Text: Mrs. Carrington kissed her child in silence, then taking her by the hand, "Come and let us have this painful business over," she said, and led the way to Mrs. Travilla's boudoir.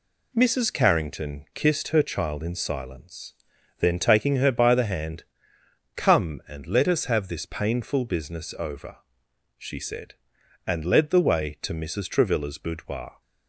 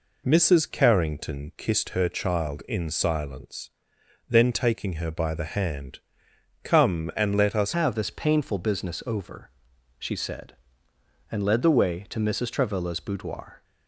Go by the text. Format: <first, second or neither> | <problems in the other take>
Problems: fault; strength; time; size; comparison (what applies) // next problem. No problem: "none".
first | changes voice at "have"; from 7.7 s on; 5.9 s long